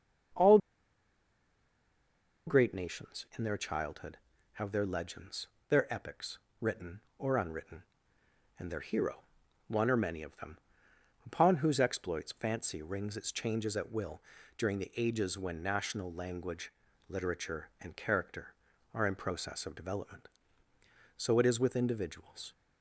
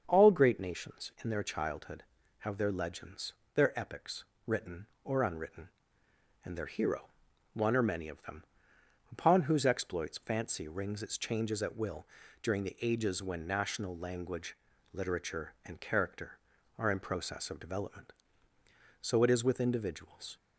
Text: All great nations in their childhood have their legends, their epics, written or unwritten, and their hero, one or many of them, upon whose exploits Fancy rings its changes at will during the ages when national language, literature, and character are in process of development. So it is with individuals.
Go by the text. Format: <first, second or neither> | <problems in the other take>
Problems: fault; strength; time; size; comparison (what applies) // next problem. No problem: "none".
second | starts louder than the rest; until 3.3 s; 7 dB; also in the second // pauses between "All" and "great"; strong; at 0.5 s; 1.8 s long // pauses between "will" and "during"; at 14.1 s; 0.38 s long; also in the second